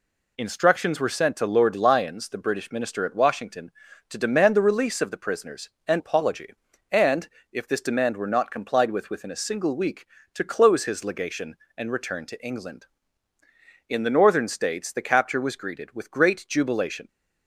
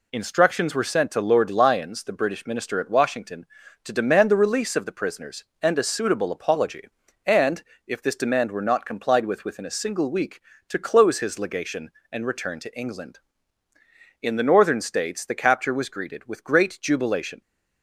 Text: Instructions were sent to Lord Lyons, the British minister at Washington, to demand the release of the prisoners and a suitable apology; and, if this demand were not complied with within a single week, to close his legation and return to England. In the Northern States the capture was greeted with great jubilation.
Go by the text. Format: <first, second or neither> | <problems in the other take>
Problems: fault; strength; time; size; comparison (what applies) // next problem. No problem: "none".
second | skips "a suitable"; at 6.0 s